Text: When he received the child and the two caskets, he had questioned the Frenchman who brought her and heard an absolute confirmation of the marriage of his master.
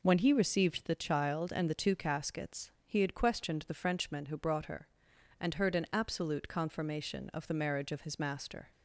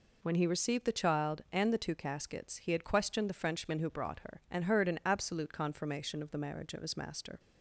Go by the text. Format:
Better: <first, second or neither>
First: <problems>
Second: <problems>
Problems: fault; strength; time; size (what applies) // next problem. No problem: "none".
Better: neither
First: none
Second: none